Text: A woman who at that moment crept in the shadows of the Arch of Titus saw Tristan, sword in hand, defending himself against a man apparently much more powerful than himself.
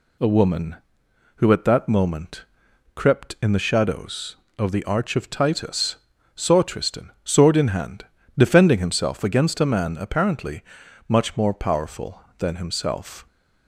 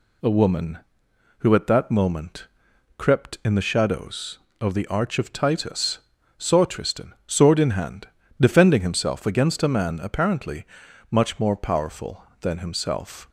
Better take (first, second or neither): neither